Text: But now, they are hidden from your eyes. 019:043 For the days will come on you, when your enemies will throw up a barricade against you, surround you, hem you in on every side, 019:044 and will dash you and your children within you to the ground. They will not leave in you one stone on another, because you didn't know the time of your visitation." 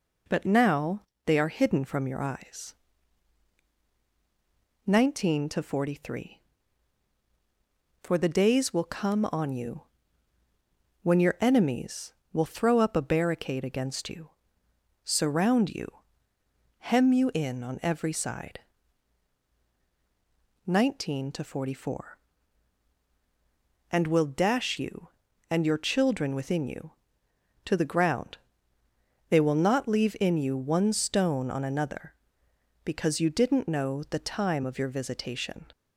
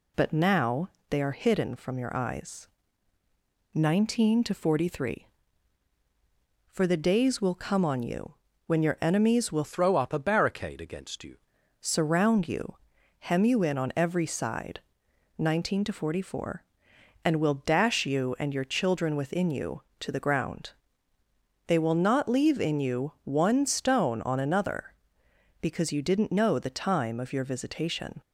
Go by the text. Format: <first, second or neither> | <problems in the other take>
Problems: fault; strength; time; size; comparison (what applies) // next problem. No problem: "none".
first | changes voice from "throw" to "you"; from 9.6 to 11.3 s; 1.7 s long